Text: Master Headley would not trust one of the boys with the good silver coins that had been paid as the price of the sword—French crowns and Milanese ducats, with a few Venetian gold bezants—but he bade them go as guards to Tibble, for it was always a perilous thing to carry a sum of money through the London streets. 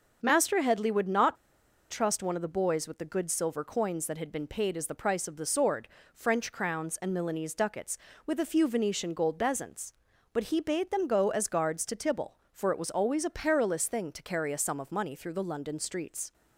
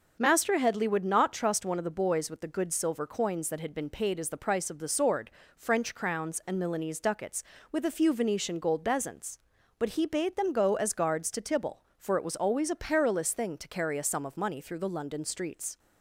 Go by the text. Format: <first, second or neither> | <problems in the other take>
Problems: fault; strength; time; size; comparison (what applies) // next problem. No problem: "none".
second | starts louder than the rest; noticeable; until 1.2 s; 6 dB; also in the second // pauses between "not" and "trust"; noticeable; at 1.3 s; 0.55 s long